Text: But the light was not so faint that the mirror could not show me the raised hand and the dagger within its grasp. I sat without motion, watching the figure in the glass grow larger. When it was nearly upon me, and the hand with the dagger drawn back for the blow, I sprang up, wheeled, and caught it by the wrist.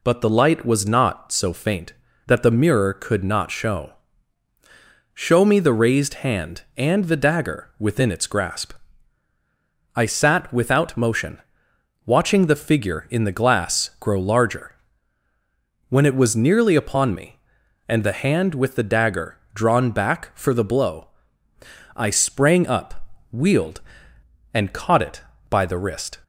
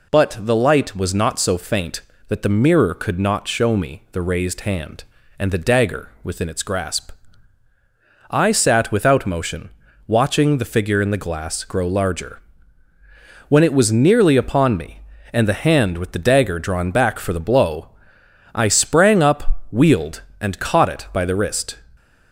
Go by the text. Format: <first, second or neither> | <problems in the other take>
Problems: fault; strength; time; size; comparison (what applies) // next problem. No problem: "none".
second | says "show" twice; at 5.1 s // pauses between "dagger" and "drawn"; slight; at 19.3 s; 0.16 s long